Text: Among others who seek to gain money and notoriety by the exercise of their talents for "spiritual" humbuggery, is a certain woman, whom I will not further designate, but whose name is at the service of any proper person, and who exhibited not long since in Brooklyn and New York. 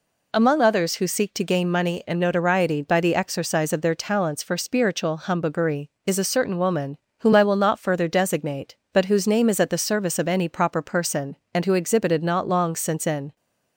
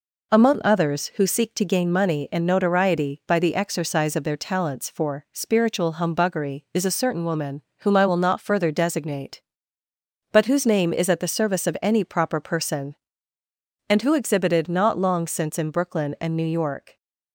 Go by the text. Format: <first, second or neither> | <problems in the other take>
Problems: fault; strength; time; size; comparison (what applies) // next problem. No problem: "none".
second | stops before "Brooklyn and New York"; at 13.3 s